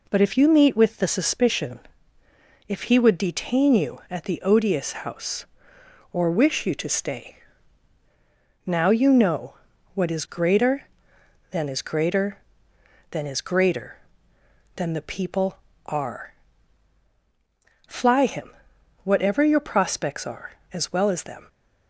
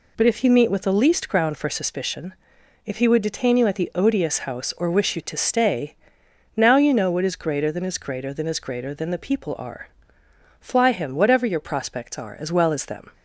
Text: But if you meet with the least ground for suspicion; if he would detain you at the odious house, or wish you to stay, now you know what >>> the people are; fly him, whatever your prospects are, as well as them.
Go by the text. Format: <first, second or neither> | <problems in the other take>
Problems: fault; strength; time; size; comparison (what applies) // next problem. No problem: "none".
second | skips "least ground for"; at 1.0 s // pauses between "know" and "what"; at 9.5 s; 0.40 s long